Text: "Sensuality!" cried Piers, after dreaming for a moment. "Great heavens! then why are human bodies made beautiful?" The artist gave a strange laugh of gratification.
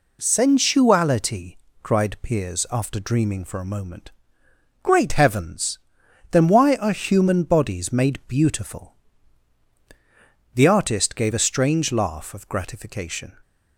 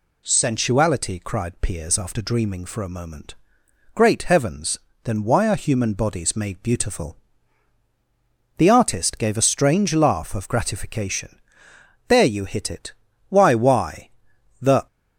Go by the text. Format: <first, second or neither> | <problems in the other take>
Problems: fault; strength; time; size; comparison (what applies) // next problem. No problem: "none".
first | goes on to say "There you hit it Why why The"; strong; from 12.0 s on; 2.8 s long